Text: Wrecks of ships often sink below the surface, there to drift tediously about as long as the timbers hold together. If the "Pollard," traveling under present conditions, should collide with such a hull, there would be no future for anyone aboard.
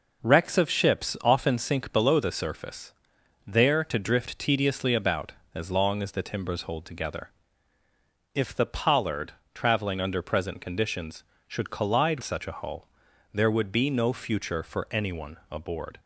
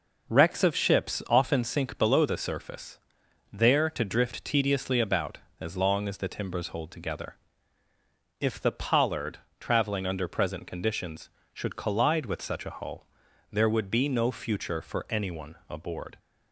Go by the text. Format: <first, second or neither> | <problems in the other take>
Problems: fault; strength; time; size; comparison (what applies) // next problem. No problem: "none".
second | skips "with"; at 12.2 s // pauses between "anyone" and "aboard"; slight; at 15.3 s; 0.16 s long; slight in the second